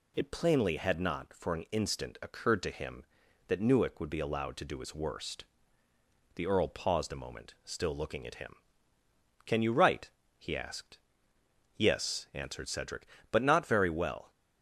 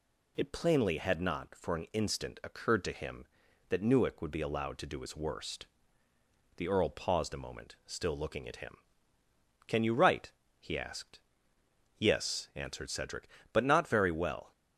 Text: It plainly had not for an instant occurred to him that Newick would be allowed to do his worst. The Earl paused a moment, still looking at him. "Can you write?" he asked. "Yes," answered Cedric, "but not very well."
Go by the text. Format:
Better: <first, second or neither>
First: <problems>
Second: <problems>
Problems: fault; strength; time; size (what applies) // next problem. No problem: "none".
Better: neither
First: none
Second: none